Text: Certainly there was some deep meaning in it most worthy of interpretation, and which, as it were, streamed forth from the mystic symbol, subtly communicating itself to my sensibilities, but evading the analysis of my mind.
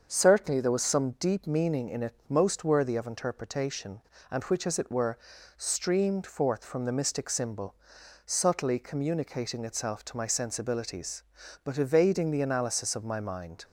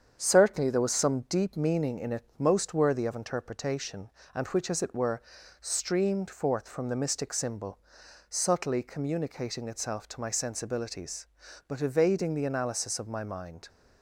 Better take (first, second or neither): first